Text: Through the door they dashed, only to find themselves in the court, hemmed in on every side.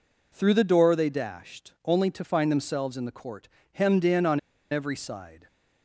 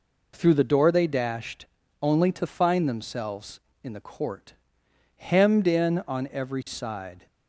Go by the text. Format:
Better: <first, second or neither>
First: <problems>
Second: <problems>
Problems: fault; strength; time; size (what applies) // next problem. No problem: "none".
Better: second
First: pauses between "on" and "every"; slight; at 4.3 s; 0.32 s long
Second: none